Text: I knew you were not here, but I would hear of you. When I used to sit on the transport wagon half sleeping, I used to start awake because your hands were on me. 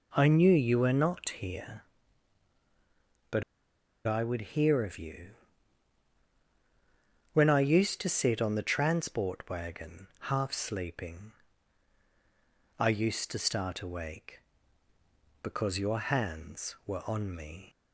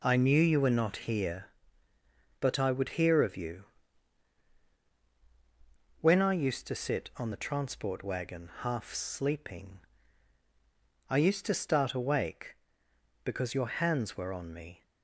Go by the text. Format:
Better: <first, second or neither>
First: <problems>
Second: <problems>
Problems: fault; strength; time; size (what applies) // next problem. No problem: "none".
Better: second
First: pauses between "but" and "I"; noticeable; at 3.4 s; 0.64 s long // pauses between "wagon" and "half"; slight; at 10.0 s; 0.24 s long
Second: none